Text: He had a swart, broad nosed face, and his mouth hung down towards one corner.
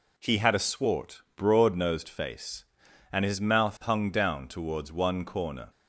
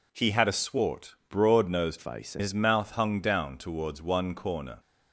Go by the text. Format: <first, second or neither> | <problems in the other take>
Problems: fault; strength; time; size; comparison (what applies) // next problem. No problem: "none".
first | changes voice from "face" to "and"; from 1.9 to 2.4 s; 0.5 s long